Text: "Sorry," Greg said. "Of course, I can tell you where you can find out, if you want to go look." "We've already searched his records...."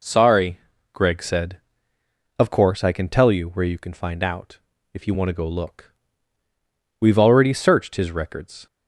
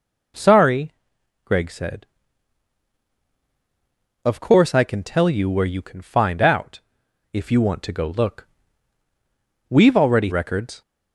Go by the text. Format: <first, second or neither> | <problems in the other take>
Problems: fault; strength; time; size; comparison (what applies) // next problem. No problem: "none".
first | skips "searched his"; at 10.3 s